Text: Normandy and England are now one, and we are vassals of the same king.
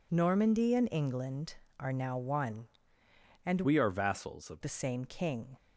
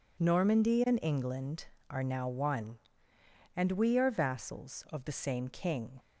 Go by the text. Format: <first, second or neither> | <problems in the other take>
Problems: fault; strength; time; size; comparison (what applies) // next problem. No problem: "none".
second | changes voice from "we" to "of"; from 3.6 to 4.6 s; 1.0 s long